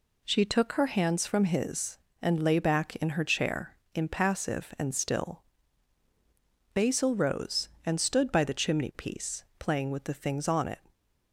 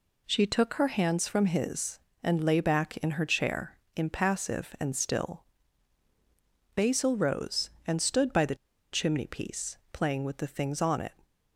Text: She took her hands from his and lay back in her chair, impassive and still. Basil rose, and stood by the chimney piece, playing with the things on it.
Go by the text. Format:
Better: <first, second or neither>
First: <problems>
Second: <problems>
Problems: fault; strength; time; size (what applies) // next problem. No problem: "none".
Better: first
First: none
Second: pauses between "the" and "chimney"; at 8.5 s; 0.37 s long